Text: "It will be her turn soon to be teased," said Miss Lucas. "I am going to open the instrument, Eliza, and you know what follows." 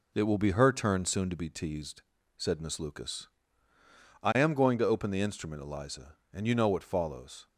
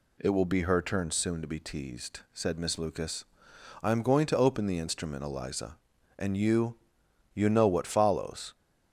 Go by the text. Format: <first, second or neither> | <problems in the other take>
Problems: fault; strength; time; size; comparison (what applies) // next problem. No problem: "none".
first | says "you" twice; at 7.3 s